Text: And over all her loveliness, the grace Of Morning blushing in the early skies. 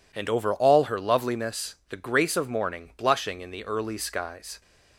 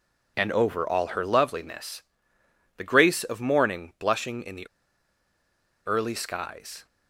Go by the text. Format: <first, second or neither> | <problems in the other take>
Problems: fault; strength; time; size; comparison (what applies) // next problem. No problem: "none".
first | pauses between "the" and "early"; at 4.6 s; 1.1 s long